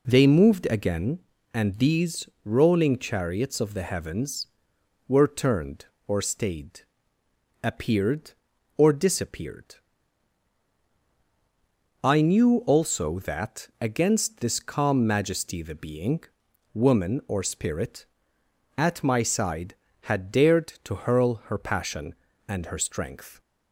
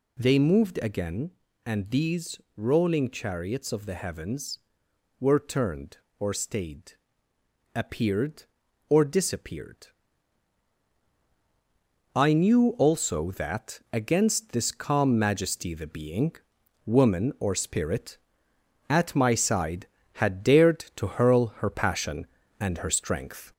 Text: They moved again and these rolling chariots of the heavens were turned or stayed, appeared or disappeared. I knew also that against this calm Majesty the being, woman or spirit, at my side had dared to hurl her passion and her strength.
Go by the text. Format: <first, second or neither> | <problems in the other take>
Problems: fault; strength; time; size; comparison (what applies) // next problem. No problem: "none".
first | gets louder; slight; throughout; 3.5 dB // pauses between "these" and "rolling"; slight; at 2.3 s; 0.16 s long; slight in the first